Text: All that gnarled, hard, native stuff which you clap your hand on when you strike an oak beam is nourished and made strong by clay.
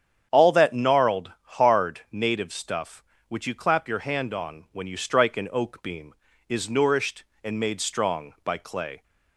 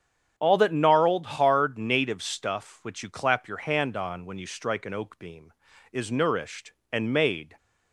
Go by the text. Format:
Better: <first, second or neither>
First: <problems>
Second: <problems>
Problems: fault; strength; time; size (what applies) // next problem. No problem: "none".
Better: first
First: starts louder than the rest; strong; until 1.4 s; 8.5 dB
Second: starts louder than the rest; strong; until 1.3 s; 8.5 dB // stops before "strong by clay"; at 7.5 s